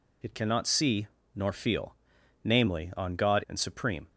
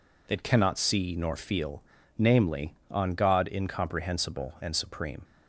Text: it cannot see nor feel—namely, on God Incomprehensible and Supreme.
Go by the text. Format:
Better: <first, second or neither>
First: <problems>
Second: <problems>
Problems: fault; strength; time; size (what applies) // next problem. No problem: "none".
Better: second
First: pauses between "see" and "nor"; slight; at 1.0 s; 0.28 s long // skips "Incomprehensible"; at 3.4 s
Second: none